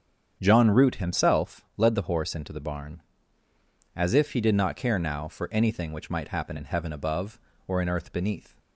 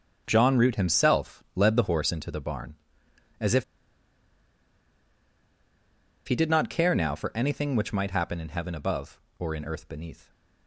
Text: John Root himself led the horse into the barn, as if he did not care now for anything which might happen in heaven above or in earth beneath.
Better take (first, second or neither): first